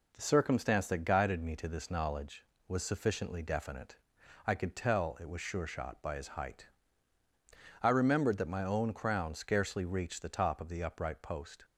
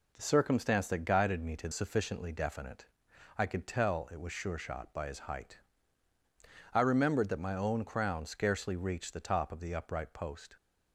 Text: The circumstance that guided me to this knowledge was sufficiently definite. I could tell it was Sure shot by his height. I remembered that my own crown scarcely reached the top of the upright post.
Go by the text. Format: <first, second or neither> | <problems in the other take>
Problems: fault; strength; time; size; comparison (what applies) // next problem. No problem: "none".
first | skips "this knowledge was"; at 1.7 s